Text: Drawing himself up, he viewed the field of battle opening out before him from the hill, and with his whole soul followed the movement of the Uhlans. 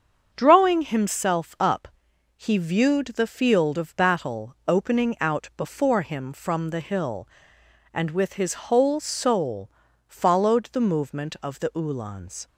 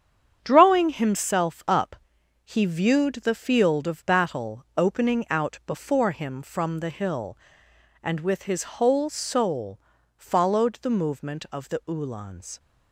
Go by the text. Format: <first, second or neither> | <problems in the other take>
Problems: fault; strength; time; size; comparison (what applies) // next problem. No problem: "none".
first | gets quieter; strong; throughout; 8 dB // starts louder than the rest; strong; until 1.4 s; 8 dB; also in the first // pauses between "soul" and "followed"; at 9.7 s; 0.38 s long; also in the first